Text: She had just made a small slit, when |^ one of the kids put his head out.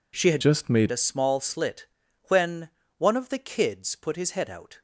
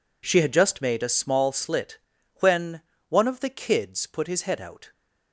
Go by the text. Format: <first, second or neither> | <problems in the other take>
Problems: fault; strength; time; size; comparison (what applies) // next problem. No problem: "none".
second | changes voice from "just" to "made"; from 0.4 to 0.9 s; 0.5 s long